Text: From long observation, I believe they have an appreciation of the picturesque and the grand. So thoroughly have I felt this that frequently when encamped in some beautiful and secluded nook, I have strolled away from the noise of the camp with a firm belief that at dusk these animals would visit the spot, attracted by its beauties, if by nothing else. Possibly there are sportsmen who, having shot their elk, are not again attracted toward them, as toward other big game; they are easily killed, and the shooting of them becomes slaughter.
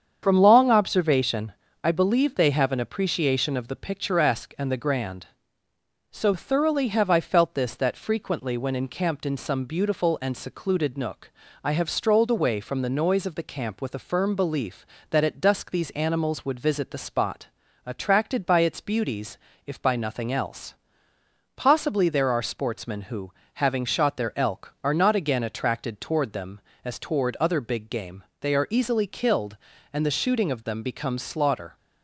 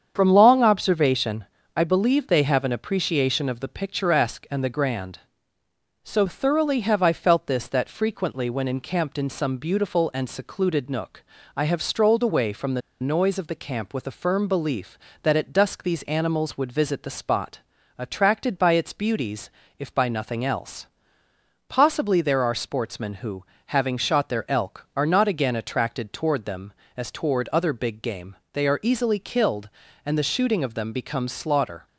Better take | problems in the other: first | starts louder than the rest; strong; until 1.1 s; 7.5 dB; strong in the first // pauses between "the" and "noise"; slight; at 12.8 s; 0.20 s long

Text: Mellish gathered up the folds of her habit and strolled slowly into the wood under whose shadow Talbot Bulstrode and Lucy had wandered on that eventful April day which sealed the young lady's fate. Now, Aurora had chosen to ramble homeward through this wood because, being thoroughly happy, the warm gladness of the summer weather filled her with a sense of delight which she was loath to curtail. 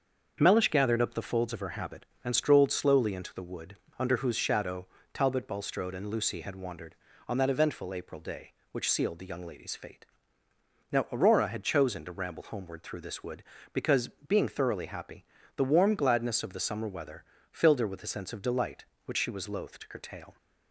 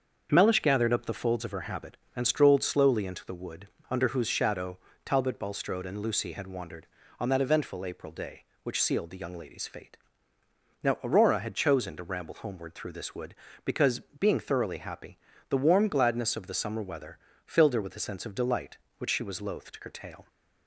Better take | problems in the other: neither | starts louder than the rest; the same in both // pauses between "wood" and "under"; slight; the same in both // pauses between "shadow" and "Talbot"; slight; the same in both // pauses between "weather" and "filled"; slight; the same in both

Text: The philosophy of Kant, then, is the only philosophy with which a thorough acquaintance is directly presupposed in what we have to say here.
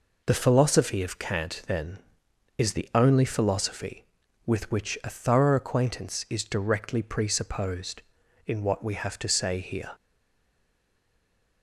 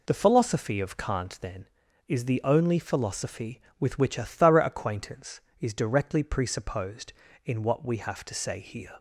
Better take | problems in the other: second | stays silent after the last word; noticeable; from 9.9 s on; 1.7 s long

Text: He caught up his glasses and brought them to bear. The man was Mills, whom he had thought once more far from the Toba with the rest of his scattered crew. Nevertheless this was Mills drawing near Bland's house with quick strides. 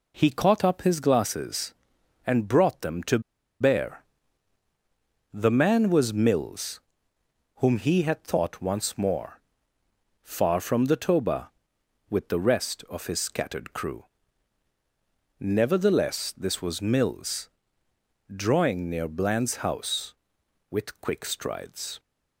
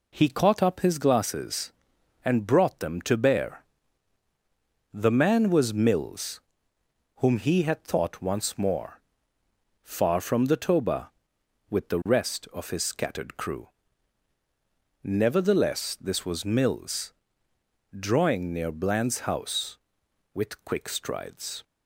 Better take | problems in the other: second | pauses between "to" and "bear"; at 3.1 s; 0.41 s long // pauses between "more" and "far"; noticeable; at 9.3 s; 0.82 s long; noticeable in the second // pauses between "Mills" and "drawing"; noticeable; at 17.4 s; 0.84 s long; noticeable in the second

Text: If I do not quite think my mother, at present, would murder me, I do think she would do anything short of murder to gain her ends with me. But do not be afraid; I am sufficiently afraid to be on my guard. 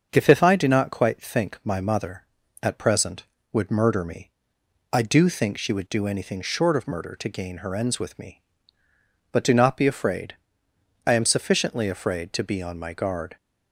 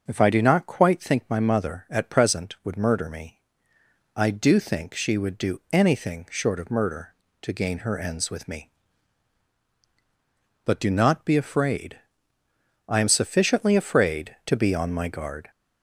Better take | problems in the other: second | starts louder than the rest; until 1.1 s; 6.5 dB; noticeable in the second // says "If" twice; at 0.2 s

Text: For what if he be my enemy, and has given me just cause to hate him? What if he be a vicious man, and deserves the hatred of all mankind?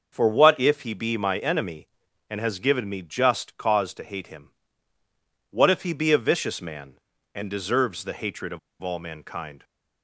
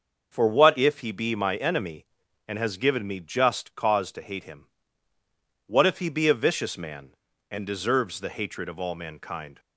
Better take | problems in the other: second | starts louder than the rest; until 1.1 s; 6.5 dB; also in the second // pauses between "of" and "all"; slight; at 8.5 s; 0.22 s long

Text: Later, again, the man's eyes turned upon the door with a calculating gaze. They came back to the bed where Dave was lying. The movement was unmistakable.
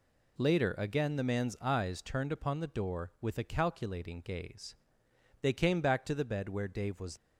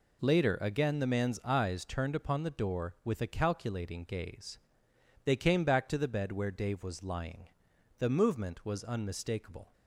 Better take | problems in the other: second | stops before "lying The movement was unmistakable"; at 7.1 s

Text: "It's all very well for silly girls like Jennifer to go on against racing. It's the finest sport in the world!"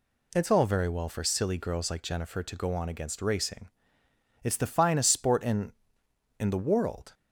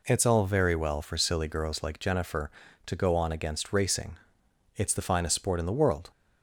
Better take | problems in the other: second | says "in" twice; at 6.3 s

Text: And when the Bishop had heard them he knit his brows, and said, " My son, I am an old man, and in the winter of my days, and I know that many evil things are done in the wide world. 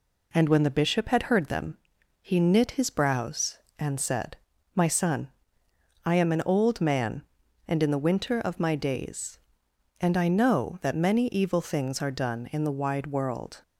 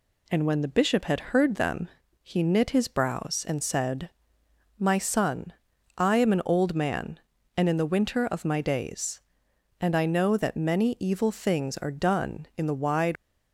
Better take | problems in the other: first | pauses between "them" and "he"; at 1.8 s; 0.40 s long; noticeable in the first // stops before "world"; at 13.1 s

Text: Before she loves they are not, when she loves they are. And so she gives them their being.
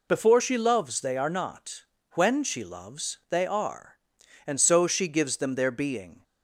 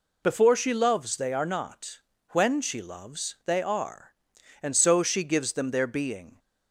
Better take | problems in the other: neither | none

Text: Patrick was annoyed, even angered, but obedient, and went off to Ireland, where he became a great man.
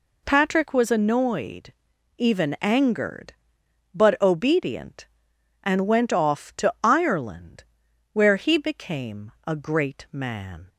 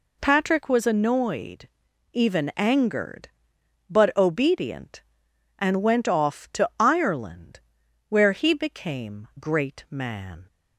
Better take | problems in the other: first | skips "a"; at 9.3 s

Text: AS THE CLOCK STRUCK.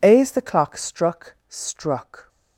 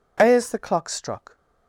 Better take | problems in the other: second | says "STRUCK" twice; at 1.5 s

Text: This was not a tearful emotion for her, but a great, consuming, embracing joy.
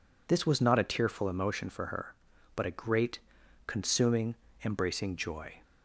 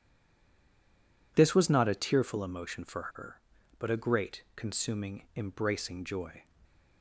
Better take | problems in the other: first | stays silent before the first word; noticeable; until 1.3 s; 1.3 s long // pauses between "for" and "her"; slight; at 3.0 s; 0.15 s long

